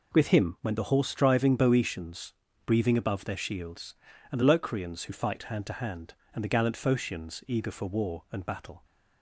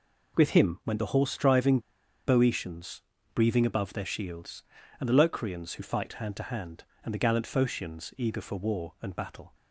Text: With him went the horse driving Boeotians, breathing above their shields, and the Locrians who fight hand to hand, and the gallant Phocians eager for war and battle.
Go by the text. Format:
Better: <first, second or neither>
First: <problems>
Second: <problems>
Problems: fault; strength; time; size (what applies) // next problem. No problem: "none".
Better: first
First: none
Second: pauses between "driving" and "Boeotians"; noticeable; at 1.7 s; 0.47 s long